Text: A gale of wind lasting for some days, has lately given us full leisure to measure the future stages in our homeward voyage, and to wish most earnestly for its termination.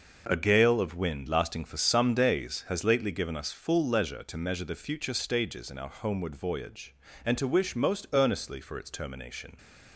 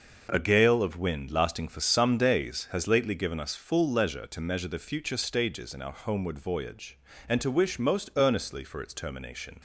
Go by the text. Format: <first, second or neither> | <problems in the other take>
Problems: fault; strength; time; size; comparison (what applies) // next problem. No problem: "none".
neither | none